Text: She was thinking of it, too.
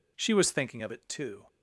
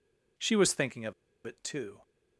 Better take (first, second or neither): first